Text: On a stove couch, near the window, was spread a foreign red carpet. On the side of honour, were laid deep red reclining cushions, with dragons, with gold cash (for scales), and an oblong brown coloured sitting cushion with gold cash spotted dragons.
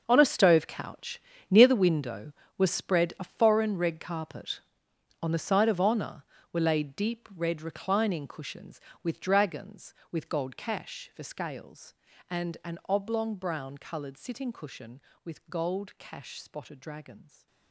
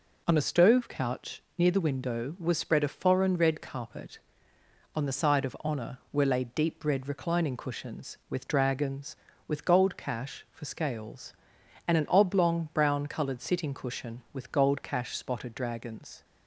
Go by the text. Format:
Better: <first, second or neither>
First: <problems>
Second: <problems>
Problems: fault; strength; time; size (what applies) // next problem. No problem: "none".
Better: second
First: gets quieter; strong; throughout; 14.5 dB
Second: none